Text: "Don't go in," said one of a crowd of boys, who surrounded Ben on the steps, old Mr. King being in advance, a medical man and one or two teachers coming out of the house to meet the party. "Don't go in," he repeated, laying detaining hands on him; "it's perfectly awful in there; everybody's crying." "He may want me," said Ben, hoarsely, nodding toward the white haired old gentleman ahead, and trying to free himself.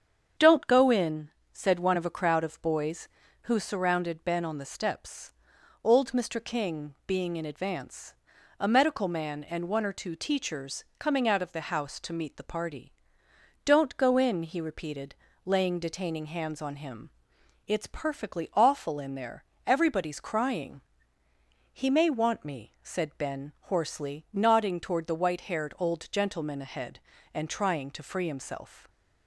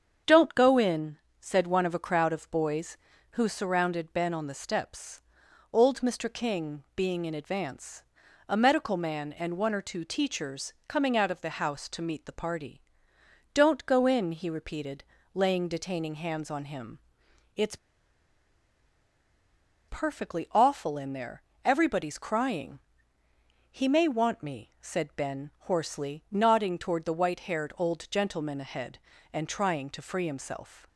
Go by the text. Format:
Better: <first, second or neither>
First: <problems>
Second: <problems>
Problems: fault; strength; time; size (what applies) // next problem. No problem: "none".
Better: first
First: starts louder than the rest; strong; until 1.5 s; 7.5 dB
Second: starts louder than the rest; strong; until 1.4 s; 7.5 dB // pauses between "it's" and "perfectly"; strong; at 17.7 s; 2.1 s long